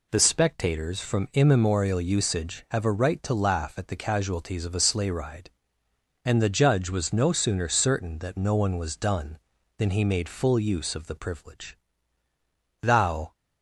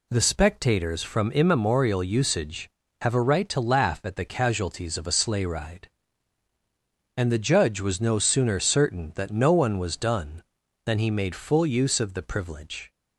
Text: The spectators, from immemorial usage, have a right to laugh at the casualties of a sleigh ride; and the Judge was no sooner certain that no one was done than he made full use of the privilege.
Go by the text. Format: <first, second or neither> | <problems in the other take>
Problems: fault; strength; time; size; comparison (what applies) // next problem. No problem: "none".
second | goes on to say "Thou"; from 12.8 s on; 0.52 s long